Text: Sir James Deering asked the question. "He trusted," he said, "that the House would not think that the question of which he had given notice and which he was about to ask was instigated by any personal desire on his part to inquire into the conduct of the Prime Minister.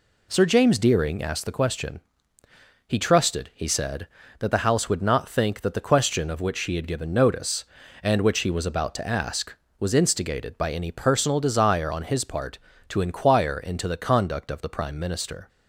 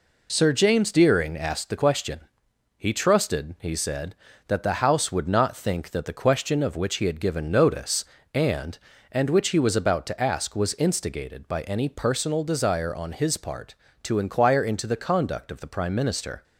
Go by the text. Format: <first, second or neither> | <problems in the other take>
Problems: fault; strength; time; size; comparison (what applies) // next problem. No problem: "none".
first | says "and" twice; at 9.1 s